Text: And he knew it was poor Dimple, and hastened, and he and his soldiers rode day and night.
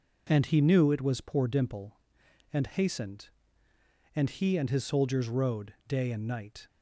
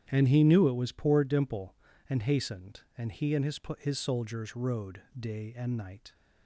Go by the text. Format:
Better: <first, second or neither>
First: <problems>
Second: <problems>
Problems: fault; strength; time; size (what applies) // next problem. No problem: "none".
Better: first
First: none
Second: starts louder than the rest; strong; until 1.1 s; 10 dB // says "his" twice; at 3.7 s // pauses between "rode" and "day"; slight; at 5.0 s; 0.18 s long